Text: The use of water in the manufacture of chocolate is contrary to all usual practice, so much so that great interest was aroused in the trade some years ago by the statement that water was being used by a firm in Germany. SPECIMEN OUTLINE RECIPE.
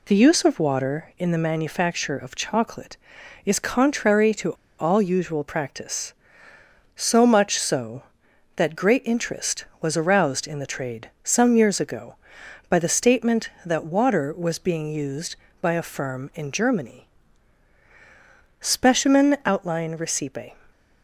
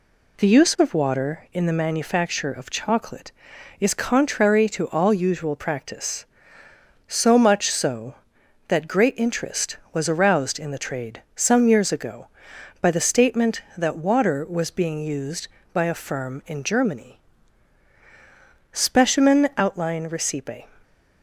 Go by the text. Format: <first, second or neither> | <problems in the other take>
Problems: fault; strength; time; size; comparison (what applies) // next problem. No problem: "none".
second | pauses between "to" and "all"; slight; at 4.5 s; 0.27 s long